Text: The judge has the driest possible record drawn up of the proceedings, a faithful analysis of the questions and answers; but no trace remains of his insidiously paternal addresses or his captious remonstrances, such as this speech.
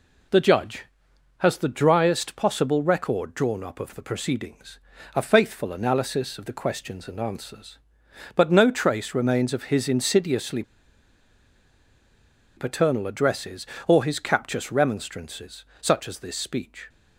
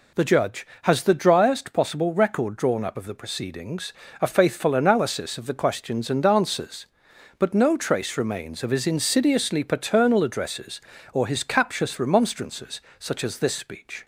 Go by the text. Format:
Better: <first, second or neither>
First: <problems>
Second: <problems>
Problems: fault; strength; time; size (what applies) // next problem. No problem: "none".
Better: second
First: pauses between "insidiously" and "paternal"; strong; at 10.6 s; 1.9 s long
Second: none